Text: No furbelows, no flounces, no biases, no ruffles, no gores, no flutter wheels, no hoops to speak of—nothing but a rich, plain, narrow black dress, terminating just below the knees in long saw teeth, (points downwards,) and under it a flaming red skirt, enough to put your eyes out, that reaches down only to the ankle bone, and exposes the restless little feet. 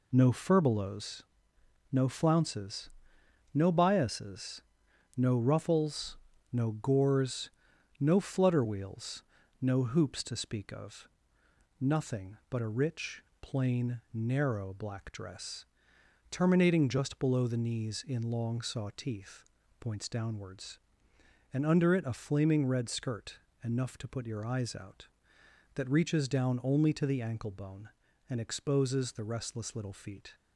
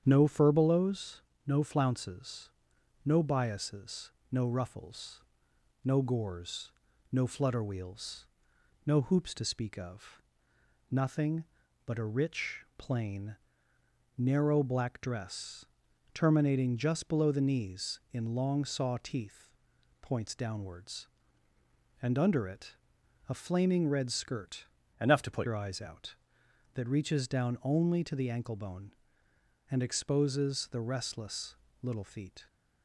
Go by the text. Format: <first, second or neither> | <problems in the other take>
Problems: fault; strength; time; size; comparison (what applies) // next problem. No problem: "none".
first | starts louder than the rest; strong; until 1.0 s; 8.5 dB // pauses between "it" and "a"; noticeable; at 22.7 s; 0.54 s long // changes voice from "enough" to "put"; from 25.0 to 25.4 s; 0.4 s long // pauses between "restless" and "little"; slight; at 31.5 s; 0.26 s long